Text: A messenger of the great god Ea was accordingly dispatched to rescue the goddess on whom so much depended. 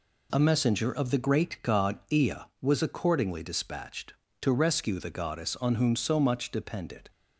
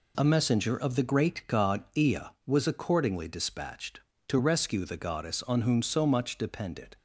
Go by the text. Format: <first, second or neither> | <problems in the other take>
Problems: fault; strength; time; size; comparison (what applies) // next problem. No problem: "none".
neither | none